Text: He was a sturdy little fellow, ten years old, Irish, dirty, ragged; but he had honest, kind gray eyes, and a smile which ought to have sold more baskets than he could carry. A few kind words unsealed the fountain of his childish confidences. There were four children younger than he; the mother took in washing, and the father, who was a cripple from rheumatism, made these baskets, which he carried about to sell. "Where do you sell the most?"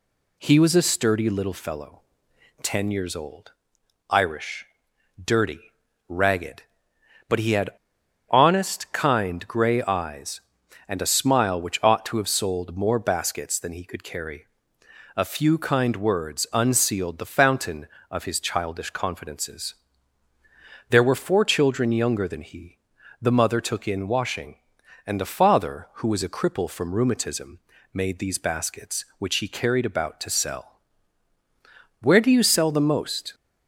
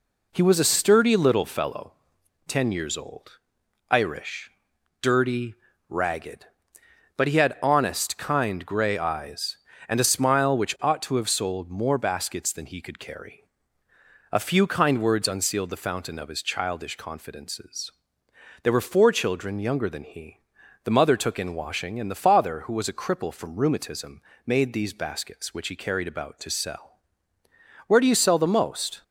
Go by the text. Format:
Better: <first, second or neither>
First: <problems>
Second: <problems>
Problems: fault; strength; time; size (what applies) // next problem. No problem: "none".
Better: second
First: pauses between "had" and "honest"; noticeable; at 7.6 s; 0.60 s long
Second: none